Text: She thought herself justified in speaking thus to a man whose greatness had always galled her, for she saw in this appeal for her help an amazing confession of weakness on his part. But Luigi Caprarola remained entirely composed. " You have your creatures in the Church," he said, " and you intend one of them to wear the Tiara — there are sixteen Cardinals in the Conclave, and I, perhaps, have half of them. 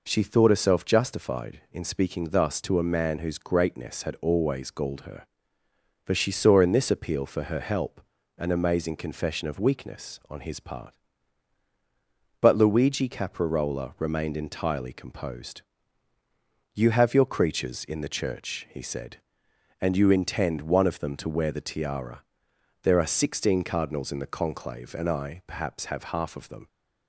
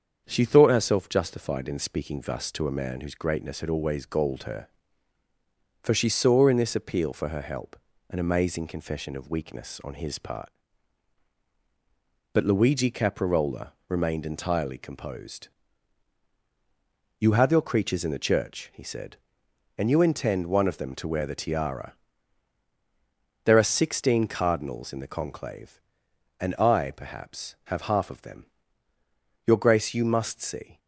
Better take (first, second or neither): first